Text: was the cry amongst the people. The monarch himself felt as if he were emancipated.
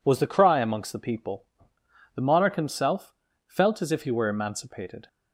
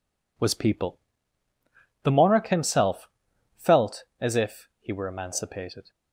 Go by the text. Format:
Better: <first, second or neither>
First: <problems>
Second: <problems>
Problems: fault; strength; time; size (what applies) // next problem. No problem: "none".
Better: first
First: pauses between "himself" and "felt"; slight; at 3.1 s; 0.34 s long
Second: skips "the cry amongst the"; at 0.5 s // pauses between "himself" and "felt"; noticeable; at 3.0 s; 0.48 s long